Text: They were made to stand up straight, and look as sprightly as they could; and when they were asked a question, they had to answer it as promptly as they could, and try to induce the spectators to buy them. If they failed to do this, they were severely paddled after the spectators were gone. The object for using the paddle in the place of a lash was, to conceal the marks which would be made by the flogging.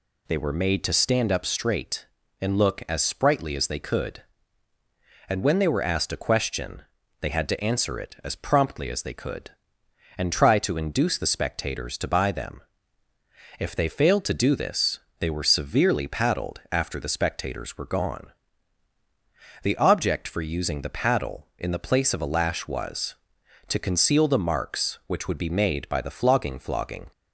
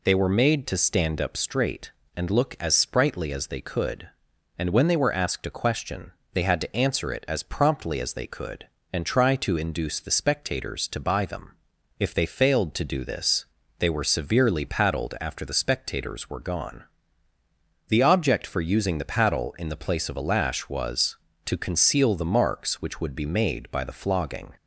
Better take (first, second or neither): second